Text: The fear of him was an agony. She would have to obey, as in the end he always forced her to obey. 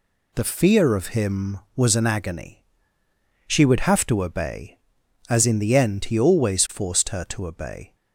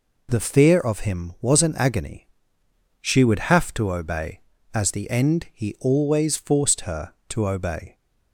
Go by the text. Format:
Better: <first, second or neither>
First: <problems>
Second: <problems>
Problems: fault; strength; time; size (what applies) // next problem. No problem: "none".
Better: first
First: none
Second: skips "in"; at 4.9 s